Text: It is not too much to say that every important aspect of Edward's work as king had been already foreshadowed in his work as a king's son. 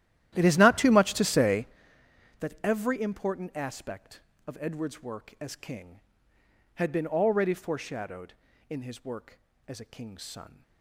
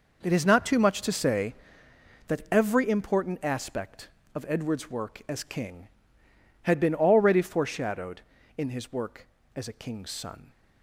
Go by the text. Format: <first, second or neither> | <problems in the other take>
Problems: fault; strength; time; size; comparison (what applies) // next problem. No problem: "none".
second | starts louder than the rest; strong; until 1.7 s; 12.5 dB